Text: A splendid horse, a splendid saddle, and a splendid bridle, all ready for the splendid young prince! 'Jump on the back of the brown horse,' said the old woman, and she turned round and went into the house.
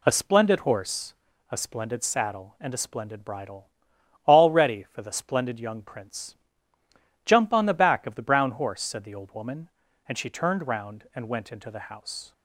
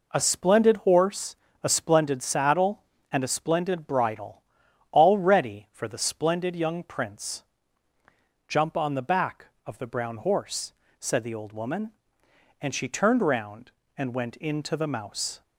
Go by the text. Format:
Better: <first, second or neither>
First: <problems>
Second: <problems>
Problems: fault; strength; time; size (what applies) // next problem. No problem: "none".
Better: first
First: none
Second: says "mouse" for "house"; at 14.8 s